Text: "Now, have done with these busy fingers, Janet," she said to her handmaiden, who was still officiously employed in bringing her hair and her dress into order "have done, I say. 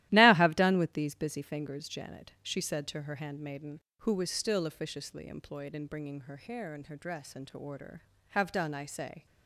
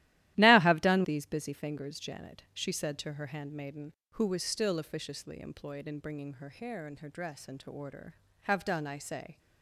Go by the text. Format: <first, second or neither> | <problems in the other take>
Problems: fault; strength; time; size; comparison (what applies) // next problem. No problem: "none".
first | starts louder than the rest; strong; until 1.3 s; 14.5 dB; strong in the first // skips "with"; at 1.0 s